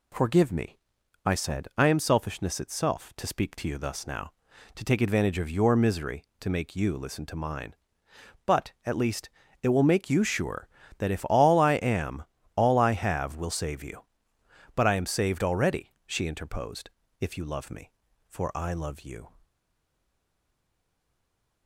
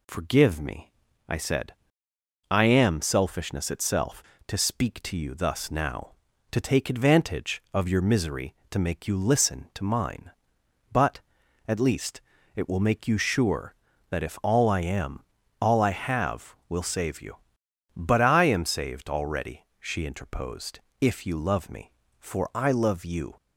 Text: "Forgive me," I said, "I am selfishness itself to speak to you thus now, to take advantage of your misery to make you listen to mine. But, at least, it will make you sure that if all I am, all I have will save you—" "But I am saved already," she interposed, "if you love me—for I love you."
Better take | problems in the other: second | stays silent after the last word; from 19.4 s on; 2.2 s long

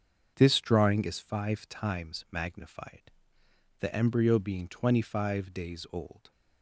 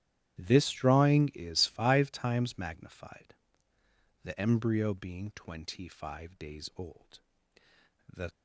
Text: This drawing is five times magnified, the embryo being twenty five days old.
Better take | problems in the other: first | starts louder than the rest; strong; until 1.4 s; 12 dB; also in the first // goes on to say "The"; slight; from 8.1 s on; 0.20 s long

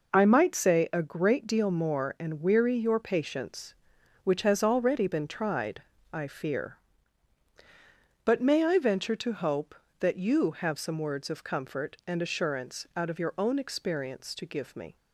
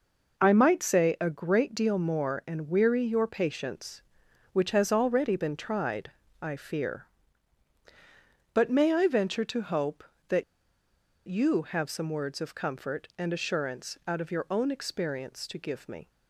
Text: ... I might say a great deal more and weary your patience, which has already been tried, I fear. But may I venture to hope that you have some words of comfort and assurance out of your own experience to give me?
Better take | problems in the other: first | pauses between "that" and "you"; noticeable; at 10.4 s; 0.84 s long

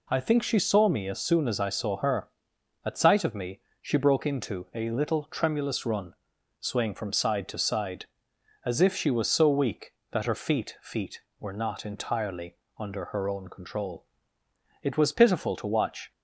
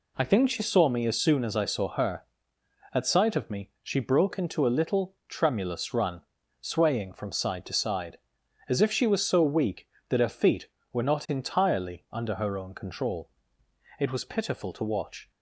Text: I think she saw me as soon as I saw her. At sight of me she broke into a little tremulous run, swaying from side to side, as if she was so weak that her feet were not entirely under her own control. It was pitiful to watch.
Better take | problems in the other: second | pauses between "me" and "she"; slight; at 3.5 s; 0.22 s long // says "feet" twice; at 10.8 s // pauses between "entirely" and "under"; slight; at 12.5 s; 0.22 s long

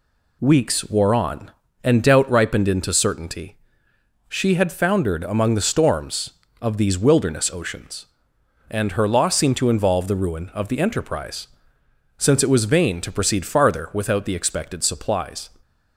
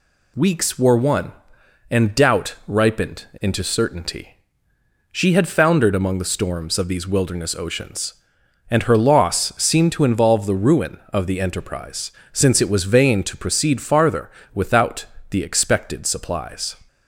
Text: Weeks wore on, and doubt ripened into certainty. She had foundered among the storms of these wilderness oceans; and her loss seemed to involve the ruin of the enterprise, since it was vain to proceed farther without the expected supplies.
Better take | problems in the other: first | says "one" for "on"; at 0.9 s // pauses between "farther" and "without"; slight; at 14.2 s; 0.24 s long // pauses between "without" and "the"; slight; at 15.0 s; 0.24 s long

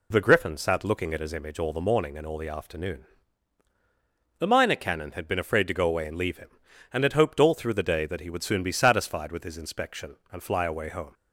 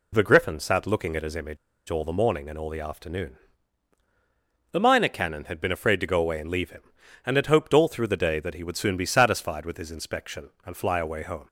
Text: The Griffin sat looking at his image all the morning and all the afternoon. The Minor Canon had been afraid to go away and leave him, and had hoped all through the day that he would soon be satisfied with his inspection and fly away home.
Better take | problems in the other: first | pauses between "image" and "all"; slight; at 1.5 s; 0.32 s long

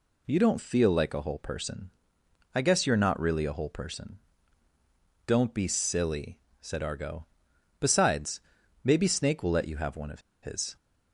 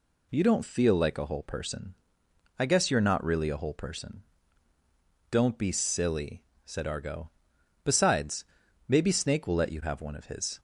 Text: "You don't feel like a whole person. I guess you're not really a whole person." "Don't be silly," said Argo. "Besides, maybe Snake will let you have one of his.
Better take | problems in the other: second | pauses between "of" and "his"; slight; at 10.2 s; 0.21 s long

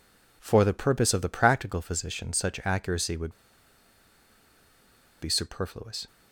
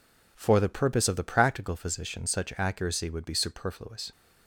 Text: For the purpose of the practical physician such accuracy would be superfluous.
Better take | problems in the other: second | pauses between "would" and "be"; strong; at 3.3 s; 1.9 s long

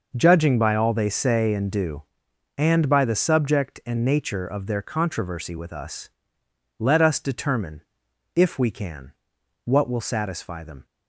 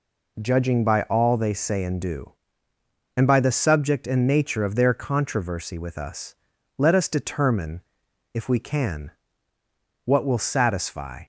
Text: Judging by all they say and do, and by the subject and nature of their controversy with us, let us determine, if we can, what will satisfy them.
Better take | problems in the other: first | stops before "them"; at 11.2 s

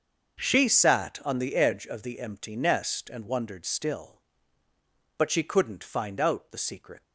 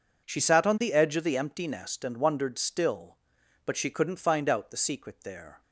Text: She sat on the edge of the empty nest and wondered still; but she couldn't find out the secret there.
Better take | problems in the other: second | starts louder than the rest; until 1.4 s; 6.5 dB // stops before "there"; at 7.0 s

